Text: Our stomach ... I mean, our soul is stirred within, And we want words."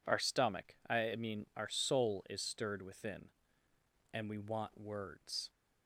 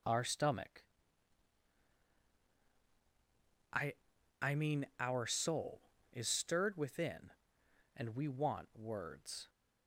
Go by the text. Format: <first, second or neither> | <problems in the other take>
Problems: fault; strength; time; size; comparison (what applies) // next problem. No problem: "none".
first | says "I" twice; at 4.4 s